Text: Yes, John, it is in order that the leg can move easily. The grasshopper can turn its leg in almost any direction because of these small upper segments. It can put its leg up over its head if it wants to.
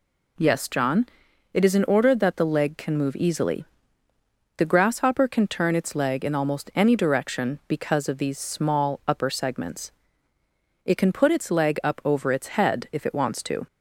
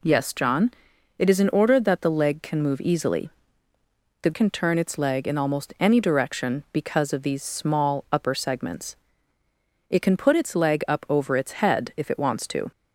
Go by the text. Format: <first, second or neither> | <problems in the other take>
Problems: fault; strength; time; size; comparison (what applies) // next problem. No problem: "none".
first | skips "grasshopper"; at 4.3 s